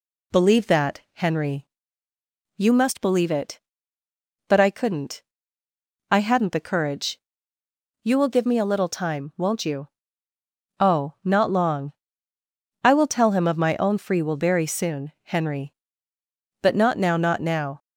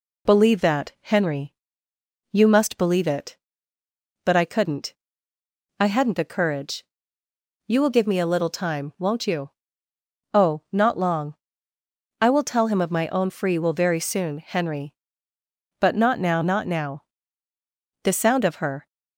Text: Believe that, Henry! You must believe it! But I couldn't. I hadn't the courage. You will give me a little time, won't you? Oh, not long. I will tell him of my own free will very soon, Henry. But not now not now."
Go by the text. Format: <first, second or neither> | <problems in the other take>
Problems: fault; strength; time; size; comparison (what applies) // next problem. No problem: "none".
first | goes on to say "The sound of her"; noticeable; from 18.0 s on; 0.84 s long